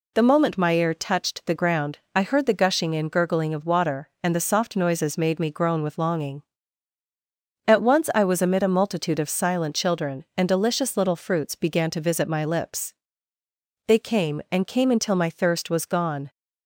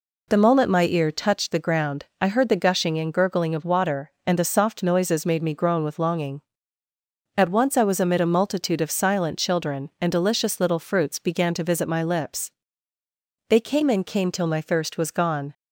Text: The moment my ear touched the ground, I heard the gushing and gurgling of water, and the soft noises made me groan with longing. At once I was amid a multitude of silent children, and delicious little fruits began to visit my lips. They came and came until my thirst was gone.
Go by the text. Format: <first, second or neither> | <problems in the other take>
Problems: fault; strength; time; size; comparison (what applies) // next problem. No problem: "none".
first | says "till" for "until"; at 14.3 s